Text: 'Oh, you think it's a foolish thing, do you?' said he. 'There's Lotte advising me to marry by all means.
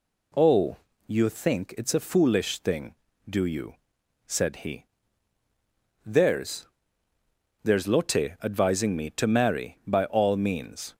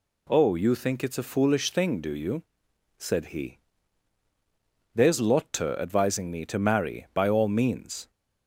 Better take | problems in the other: second | says "There's" twice; at 7.6 s

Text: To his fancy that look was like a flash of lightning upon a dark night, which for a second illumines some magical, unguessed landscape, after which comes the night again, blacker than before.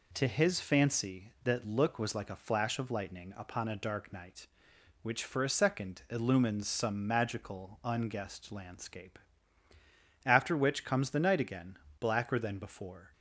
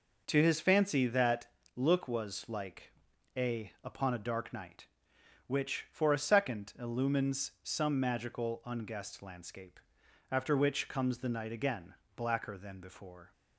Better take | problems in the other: first | pauses between "that" and "look"; slight; at 1.4 s; 0.28 s long // pauses between "like" and "a"; at 2.9 s; 0.44 s long // skips "flash of lightning"; at 3.7 s

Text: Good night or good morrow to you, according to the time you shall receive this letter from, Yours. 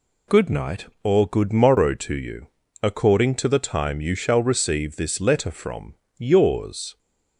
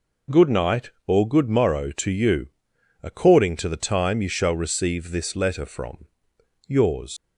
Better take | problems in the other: first | leaves "Yours" unfinished; at 7.1 s; 125 ms

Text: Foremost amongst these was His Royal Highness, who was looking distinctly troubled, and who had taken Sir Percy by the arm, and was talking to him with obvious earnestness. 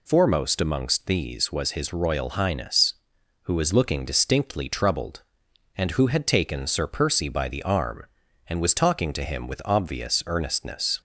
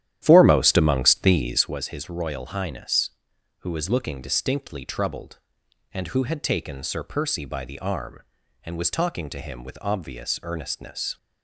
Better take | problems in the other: first | starts louder than the rest; strong; until 1.8 s; 11.5 dB

